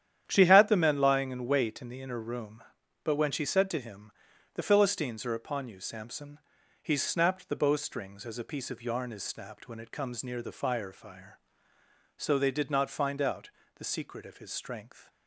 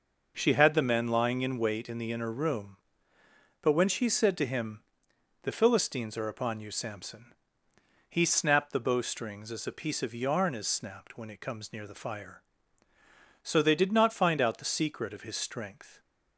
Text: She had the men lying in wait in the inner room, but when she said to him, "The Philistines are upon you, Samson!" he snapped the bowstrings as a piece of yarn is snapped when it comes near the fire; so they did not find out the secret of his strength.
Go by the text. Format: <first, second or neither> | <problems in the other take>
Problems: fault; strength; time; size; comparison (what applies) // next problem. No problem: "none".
second | starts louder than the rest; strong; until 1.2 s; 10 dB // says "fire" twice; at 10.9 s // pauses between "out" and "the"; slight; at 13.4 s; 0.26 s long